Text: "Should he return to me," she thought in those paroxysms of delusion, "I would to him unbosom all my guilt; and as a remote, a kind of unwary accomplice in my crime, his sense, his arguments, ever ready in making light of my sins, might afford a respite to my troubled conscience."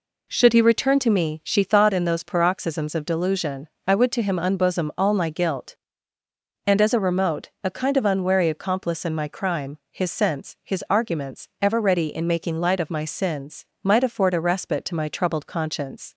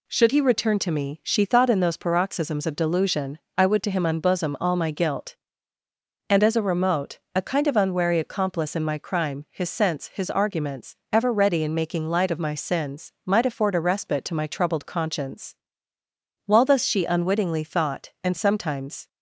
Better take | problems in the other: first | goes on to say "While thus she unwittingly thought and sometimes"; strong; from 16.4 s on; 2.6 s long

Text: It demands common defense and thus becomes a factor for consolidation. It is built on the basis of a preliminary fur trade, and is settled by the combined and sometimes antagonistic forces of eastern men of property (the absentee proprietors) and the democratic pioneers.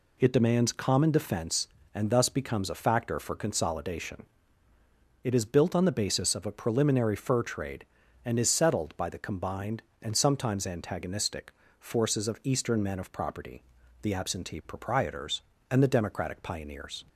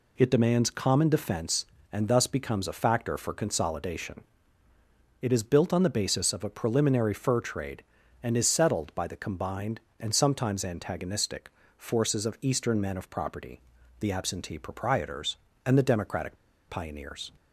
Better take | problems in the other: first | pauses between "antagonistic" and "forces"; slight; at 11.4 s; 0.28 s long; slight in the first // pauses between "democratic" and "pioneers"; slight; at 16.3 s; 0.34 s long

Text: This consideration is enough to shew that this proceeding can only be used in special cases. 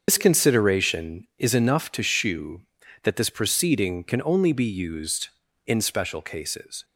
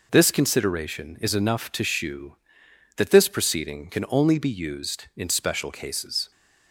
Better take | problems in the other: second | loses the start of "This"; at 0.0 s; 65 ms // starts louder than the rest; until 1.0 s; 6.5 dB

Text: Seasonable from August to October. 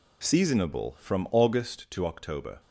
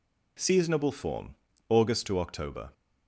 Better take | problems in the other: first | says "form" for "from"; at 0.9 s

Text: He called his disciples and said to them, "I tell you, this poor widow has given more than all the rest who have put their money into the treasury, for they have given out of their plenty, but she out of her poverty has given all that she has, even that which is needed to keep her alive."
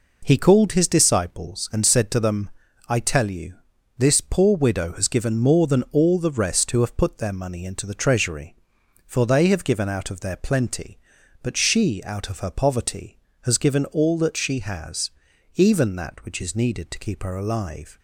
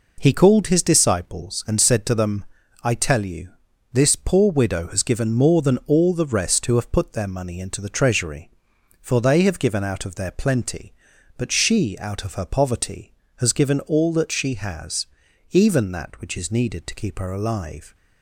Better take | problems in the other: neither | none

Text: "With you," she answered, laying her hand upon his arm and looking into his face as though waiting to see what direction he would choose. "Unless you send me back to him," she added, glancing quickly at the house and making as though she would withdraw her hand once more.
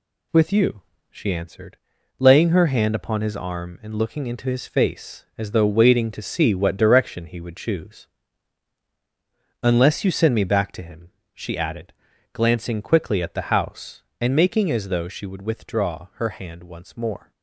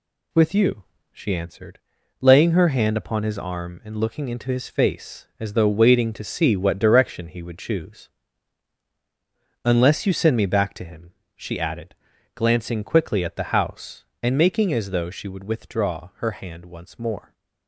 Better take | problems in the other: neither | none

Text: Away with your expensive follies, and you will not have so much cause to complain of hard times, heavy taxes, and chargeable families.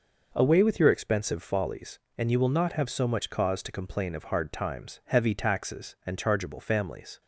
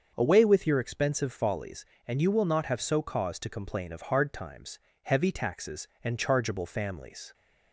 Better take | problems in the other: first | starts louder than the rest; until 1.1 s; 6.5 dB // skips "much"; at 3.0 s

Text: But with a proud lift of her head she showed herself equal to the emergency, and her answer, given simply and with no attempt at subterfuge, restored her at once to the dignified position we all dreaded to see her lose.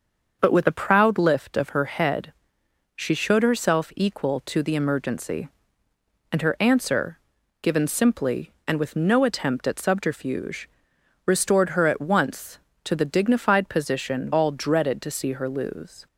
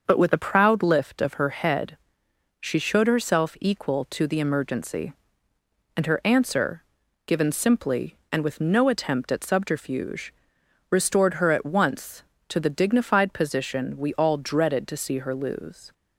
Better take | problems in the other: second | starts louder than the rest; until 1.4 s; 6.5 dB; also in the second // pauses between "head" and "she"; noticeable; at 2.3 s; 0.64 s long; noticeable in the second // skips "we"; at 14.3 s

